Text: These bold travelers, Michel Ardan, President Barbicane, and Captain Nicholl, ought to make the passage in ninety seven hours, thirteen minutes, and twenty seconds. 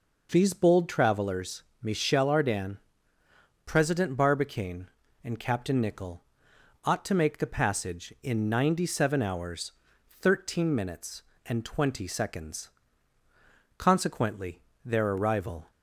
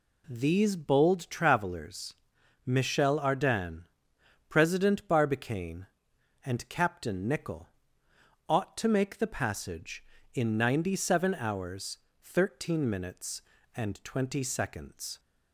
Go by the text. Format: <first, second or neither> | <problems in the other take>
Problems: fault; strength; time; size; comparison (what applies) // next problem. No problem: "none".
second | goes on to say "Consequently their arrival"; strong; from 13.7 s on; 1.9 s long